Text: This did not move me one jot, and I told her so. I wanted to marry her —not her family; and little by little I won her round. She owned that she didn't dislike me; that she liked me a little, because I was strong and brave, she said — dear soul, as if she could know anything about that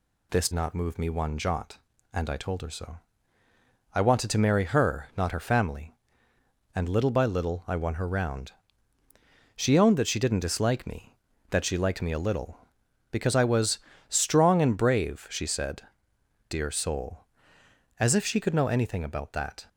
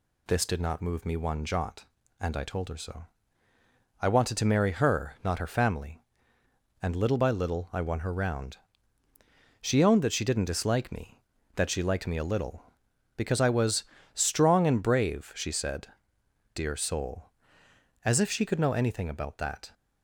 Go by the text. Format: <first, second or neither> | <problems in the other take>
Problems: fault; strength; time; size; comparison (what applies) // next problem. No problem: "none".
second | skips "did"; at 0.5 s // pauses between "was" and "strong"; slight; at 13.7 s; 0.30 s long; slight in the second